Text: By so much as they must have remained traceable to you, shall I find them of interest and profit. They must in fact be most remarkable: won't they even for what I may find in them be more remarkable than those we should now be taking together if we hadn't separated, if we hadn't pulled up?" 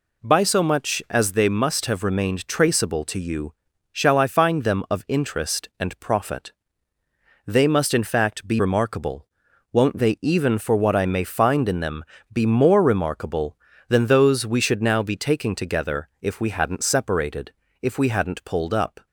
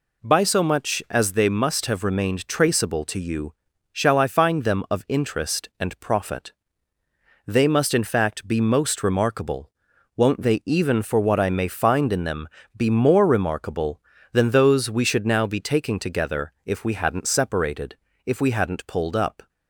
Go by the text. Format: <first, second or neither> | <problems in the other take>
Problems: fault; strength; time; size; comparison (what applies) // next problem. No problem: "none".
second | skips "most"; at 8.5 s // pauses between "them" and "be"; slight; at 12.0 s; 0.26 s long; slight in the second